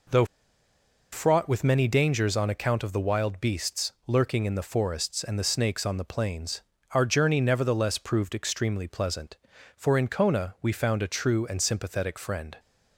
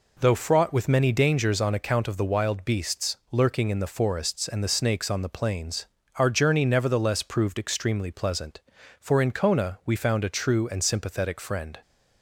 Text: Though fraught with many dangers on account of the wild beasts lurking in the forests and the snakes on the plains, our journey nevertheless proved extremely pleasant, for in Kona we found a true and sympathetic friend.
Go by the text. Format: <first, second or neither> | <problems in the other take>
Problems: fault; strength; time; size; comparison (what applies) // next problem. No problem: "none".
second | pauses between "Though" and "fraught"; noticeable; at 0.2 s; 0.88 s long